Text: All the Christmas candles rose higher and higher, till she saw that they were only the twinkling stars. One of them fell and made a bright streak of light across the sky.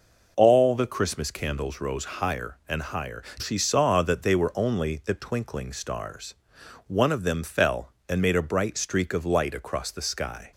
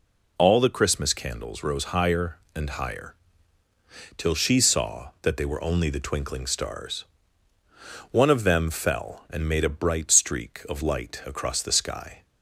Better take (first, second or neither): second